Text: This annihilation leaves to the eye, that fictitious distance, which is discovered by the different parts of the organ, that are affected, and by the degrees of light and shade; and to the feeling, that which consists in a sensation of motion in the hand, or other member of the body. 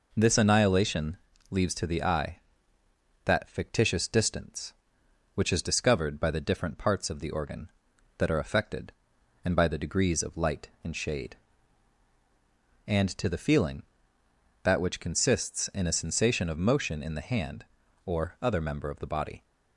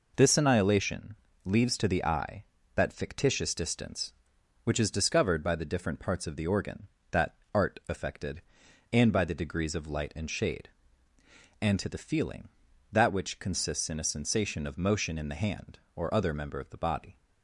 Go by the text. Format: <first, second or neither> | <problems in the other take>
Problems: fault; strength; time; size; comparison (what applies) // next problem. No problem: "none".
first | pauses between "annihilation" and "leaves"; slight; at 1.1 s; 0.26 s long; slight in the first // says "art" for "are"; at 7.5 s